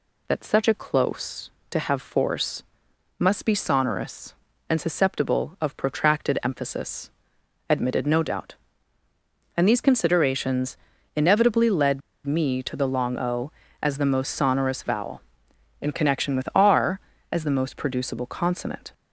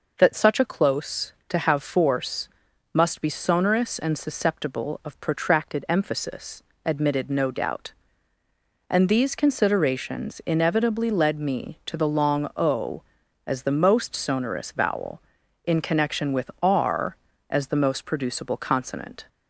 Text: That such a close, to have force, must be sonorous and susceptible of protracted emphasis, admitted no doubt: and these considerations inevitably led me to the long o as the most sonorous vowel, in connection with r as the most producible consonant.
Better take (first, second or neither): second